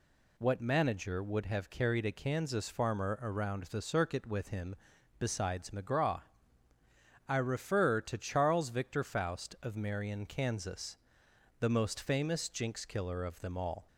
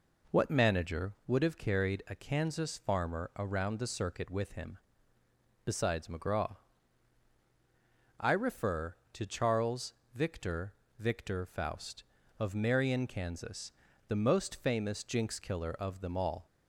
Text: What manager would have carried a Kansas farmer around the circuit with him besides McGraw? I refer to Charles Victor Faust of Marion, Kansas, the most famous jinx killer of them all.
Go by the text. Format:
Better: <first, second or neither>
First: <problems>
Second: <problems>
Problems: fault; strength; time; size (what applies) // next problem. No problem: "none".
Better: first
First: pauses between "him" and "besides"; at 4.7 s; 0.44 s long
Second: pauses between "him" and "besides"; noticeable; at 4.7 s; 0.86 s long // pauses between "Charles" and "Victor"; slight; at 9.9 s; 0.20 s long // says "Victor" twice; at 10.9 s